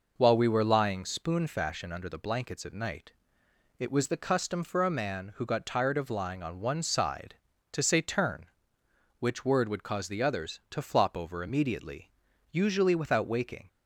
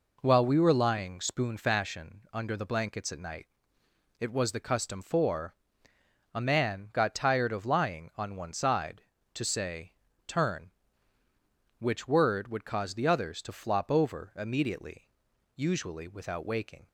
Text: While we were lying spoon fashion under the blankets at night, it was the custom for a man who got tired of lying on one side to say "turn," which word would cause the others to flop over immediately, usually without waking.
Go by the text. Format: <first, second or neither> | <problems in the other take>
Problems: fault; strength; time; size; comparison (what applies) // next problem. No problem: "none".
first | pauses between "for" and "a"; noticeable; at 5.5 s; 0.82 s long // skips "who"; at 6.9 s // pauses between "say" and "turn"; slight; at 9.9 s; 0.34 s long